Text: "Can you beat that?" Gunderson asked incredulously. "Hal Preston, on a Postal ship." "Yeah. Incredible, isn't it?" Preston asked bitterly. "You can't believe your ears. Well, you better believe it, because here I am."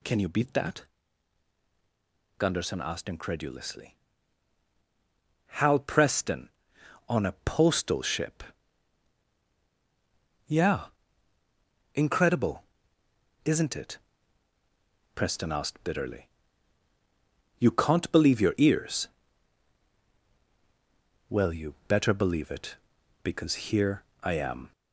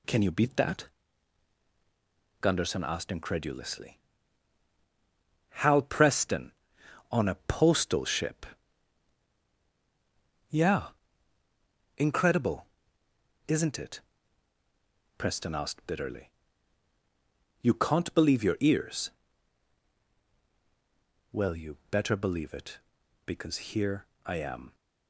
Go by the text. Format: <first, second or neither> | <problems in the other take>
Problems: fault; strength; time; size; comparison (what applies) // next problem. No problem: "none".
second | gets louder; slight; throughout; 2 dB // pauses between "here" and "I"; slight; at 24.0 s; 0.20 s long; slight in the second